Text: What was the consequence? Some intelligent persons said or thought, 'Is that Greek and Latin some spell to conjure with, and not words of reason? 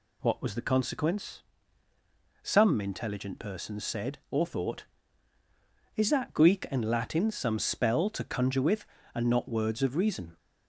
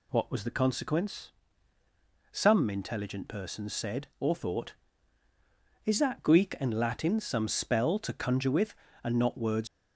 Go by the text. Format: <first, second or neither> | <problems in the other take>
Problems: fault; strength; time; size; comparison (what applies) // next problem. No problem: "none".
first | stops before "of reason"; at 9.6 s